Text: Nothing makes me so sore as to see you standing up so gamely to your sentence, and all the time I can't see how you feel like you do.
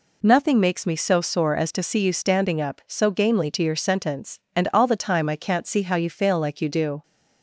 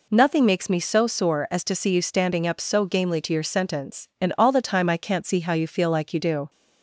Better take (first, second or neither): second